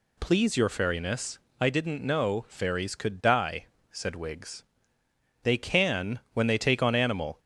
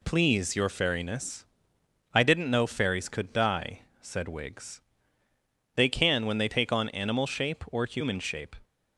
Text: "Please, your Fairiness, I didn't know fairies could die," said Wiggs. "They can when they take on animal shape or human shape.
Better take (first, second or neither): second